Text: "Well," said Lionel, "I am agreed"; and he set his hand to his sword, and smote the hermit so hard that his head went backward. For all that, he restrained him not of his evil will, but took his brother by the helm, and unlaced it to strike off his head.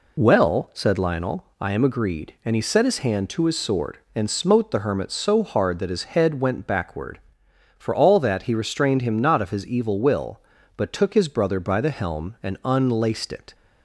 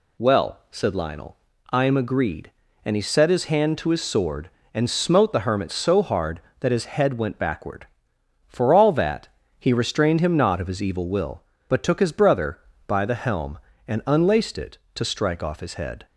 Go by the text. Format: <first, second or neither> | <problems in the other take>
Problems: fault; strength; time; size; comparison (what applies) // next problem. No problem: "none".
second | stops before "to strike off his head"; at 13.5 s